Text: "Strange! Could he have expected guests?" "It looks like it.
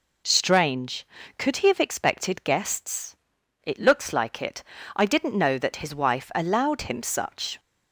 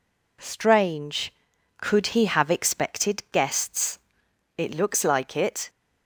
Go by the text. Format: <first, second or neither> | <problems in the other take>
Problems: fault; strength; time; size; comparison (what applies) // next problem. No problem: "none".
second | goes on to say "I didn't know that his wife allowed him such"; strong; from 4.9 s on; 2.6 s long